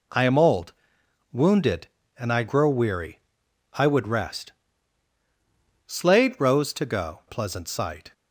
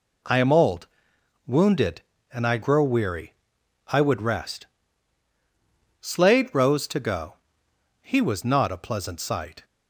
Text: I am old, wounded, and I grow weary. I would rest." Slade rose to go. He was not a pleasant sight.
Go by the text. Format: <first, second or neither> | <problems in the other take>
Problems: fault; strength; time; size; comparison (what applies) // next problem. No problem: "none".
second | skips "He was not a"; at 7.2 s